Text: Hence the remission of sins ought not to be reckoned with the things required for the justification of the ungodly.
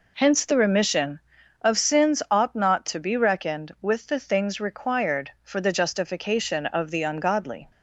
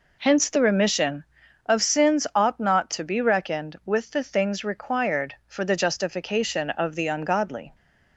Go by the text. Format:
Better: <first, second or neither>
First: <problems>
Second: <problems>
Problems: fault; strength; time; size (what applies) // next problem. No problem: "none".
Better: neither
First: none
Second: none